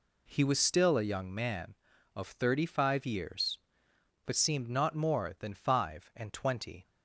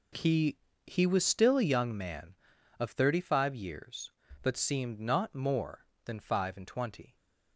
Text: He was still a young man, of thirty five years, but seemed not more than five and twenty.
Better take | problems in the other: first | says "He" twice; at 0.8 s

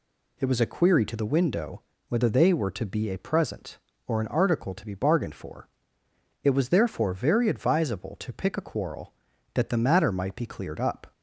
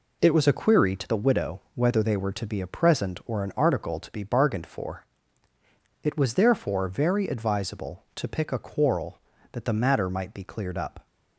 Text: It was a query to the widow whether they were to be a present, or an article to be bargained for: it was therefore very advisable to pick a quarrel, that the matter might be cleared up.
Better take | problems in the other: second | says "window" for "widow"; at 1.2 s

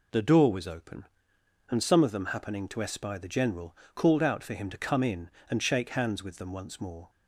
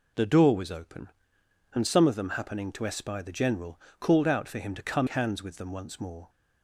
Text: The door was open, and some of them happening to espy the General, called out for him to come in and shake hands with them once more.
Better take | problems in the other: first | skips "in and shake"; at 5.0 s

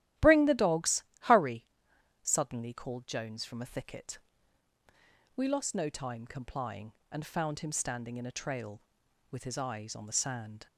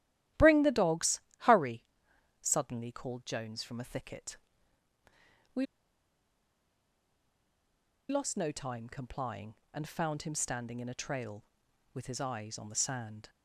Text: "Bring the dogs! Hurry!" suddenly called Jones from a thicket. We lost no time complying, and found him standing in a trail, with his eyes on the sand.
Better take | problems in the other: first | starts louder than the rest; strong; until 1.5 s; 13.5 dB; strong in the first // pauses between "We" and "lost"; strong; at 5.6 s; 2.4 s long

